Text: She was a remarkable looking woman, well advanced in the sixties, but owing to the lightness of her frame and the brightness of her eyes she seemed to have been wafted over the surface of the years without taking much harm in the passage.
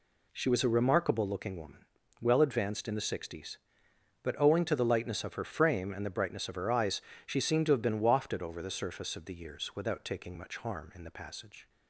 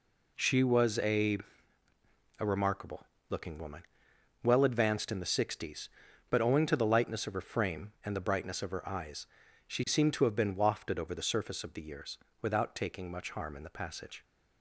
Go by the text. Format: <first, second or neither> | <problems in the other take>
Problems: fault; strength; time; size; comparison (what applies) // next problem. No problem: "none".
first | says "a" twice; at 2.3 s // pauses between "remarkable" and "looking"; slight; at 3.0 s; 0.24 s long // pauses between "eyes" and "she"; at 9.2 s; 0.40 s long; slight in the first // pauses between "years" and "without"; slight; at 12.1 s; 0.24 s long